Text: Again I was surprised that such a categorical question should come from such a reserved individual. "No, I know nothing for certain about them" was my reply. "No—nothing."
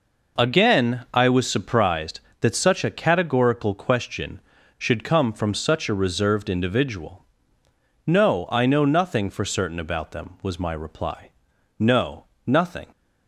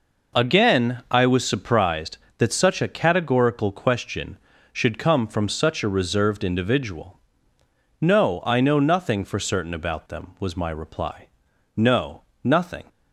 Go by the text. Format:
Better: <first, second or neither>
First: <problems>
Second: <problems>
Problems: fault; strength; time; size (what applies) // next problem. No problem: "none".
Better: neither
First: none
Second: none